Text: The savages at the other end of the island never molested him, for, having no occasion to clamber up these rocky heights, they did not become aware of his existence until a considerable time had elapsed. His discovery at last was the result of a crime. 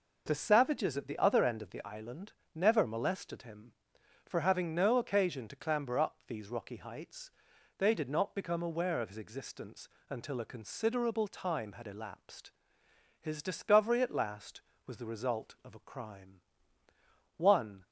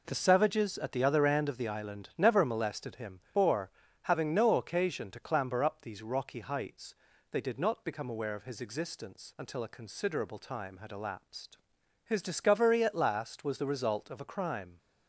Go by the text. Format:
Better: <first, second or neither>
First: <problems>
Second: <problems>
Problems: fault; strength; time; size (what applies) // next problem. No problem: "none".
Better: second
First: pauses between "island" and "never"; slight; at 2.3 s; 0.20 s long // pauses between "existence" and "until"; slight; at 9.8 s; 0.22 s long // goes on to say "One"; slight; from 17.3 s on; 0.48 s long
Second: none